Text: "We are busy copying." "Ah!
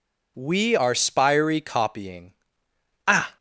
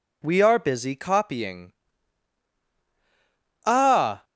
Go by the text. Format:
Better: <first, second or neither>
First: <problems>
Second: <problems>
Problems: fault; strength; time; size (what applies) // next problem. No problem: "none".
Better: second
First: says "spiry" for "busy"; at 0.9 s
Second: none